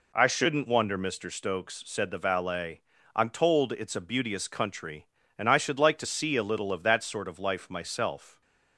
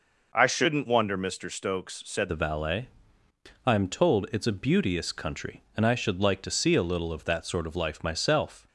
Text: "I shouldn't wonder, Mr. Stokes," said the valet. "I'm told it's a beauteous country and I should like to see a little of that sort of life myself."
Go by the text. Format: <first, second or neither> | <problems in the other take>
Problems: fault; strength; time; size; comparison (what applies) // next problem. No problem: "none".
first | changes voice at "the"; from 2.2 s on; 6.4 s long